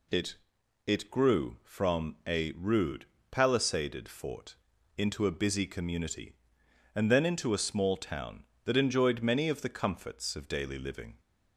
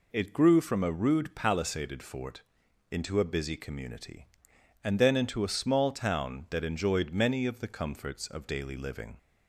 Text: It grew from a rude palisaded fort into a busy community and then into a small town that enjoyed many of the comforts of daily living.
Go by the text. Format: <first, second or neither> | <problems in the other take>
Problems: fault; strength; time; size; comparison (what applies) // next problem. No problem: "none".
second | says "It" twice; at 0.8 s // pauses between "rude" and "palisaded"; slight; at 3.0 s; 0.24 s long // pauses between "fort" and "into"; at 4.5 s; 0.42 s long; noticeable in the second